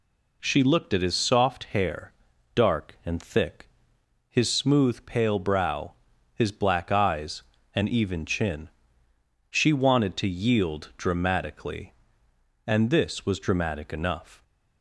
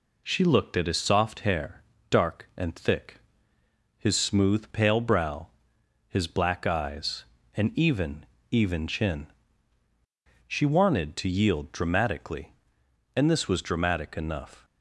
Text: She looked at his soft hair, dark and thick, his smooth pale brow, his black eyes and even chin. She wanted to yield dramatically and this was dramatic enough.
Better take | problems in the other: first | says "even" twice; at 8.5 s

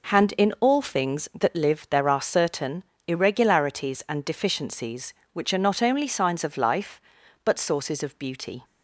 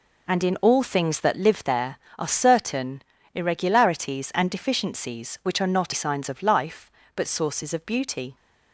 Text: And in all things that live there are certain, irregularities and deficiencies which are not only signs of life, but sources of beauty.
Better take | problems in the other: first | skips "only"; at 5.9 s

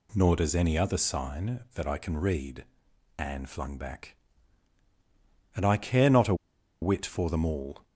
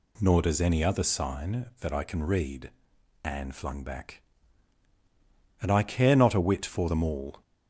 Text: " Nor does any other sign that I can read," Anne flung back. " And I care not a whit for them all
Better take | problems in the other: second | pauses between "a" and "whit"; noticeable; at 6.3 s; 0.47 s long

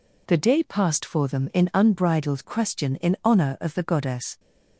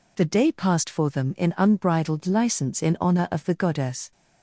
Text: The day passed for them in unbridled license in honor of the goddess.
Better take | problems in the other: second | says "question" for "license"; at 2.4 s

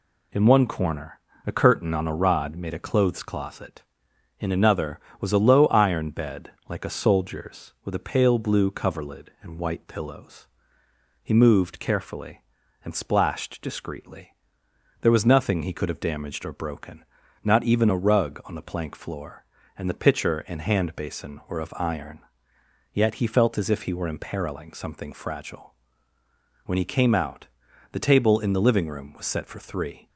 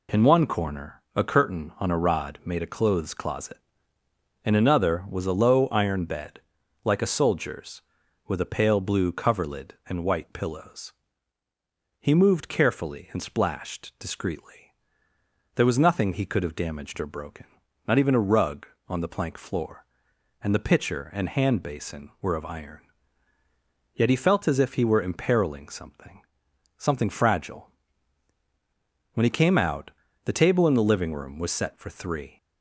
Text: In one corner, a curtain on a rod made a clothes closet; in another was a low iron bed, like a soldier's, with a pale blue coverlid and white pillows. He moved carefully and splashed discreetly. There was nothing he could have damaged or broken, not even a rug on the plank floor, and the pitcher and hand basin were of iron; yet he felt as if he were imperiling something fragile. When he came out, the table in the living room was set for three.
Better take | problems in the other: first | says "something" twice; at 26.7 s

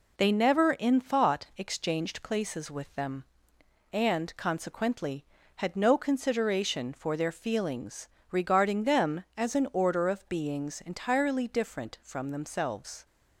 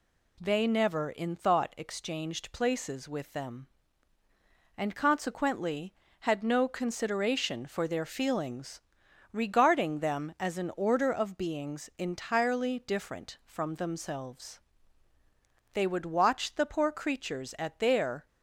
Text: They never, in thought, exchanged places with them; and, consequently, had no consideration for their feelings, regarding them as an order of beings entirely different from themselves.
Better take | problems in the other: first | goes on to say "They would watch the poor creatures at their"; strong; from 15.7 s on; 2.5 s long

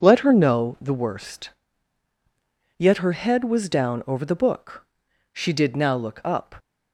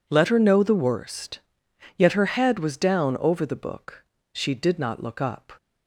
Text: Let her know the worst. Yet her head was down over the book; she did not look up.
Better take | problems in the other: second | says "now" for "not"; at 5.7 s

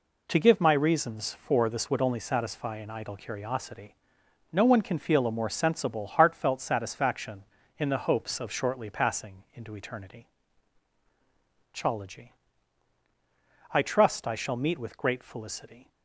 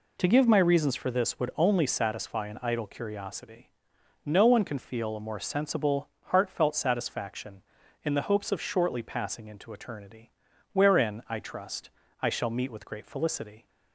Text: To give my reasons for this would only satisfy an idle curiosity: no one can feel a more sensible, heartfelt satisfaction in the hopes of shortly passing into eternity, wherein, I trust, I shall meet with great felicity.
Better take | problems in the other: second | says "chology" for "wherein"; at 11.7 s

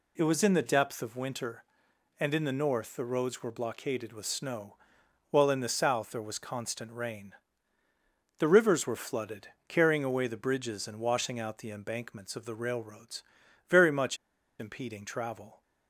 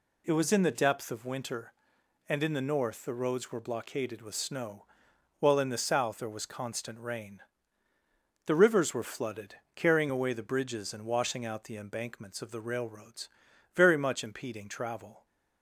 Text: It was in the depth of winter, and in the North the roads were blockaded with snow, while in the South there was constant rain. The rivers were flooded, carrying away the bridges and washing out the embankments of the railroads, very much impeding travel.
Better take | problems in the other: second | pauses between "much" and "impeding"; at 14.1 s; 0.43 s long

